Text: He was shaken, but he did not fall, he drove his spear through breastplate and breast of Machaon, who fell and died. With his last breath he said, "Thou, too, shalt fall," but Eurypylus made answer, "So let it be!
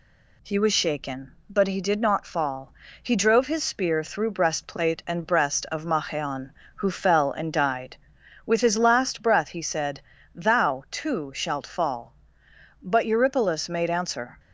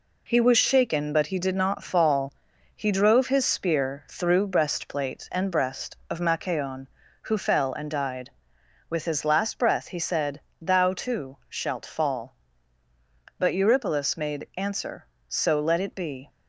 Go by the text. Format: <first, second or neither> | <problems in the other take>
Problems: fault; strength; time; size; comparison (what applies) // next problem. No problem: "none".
second | stops before "So let it be"; at 14.3 s